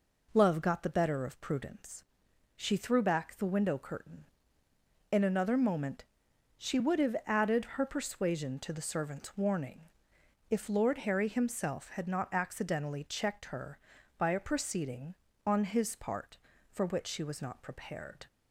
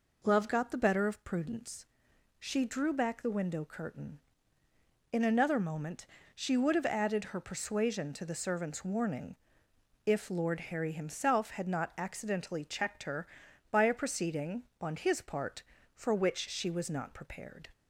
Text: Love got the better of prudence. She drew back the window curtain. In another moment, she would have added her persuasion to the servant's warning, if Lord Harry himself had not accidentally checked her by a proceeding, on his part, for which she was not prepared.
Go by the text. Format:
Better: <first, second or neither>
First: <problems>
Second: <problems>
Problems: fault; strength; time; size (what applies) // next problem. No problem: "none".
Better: second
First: says "threw" for "drew"; at 2.7 s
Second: none